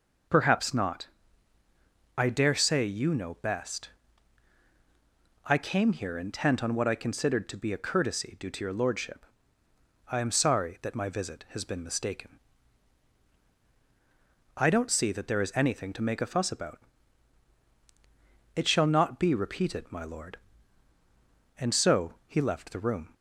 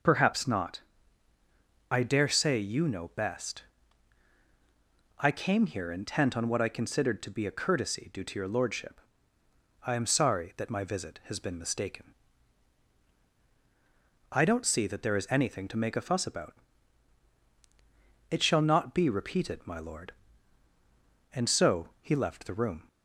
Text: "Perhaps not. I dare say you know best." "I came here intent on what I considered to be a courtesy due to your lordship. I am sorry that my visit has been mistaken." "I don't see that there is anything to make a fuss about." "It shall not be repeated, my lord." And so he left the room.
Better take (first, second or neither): neither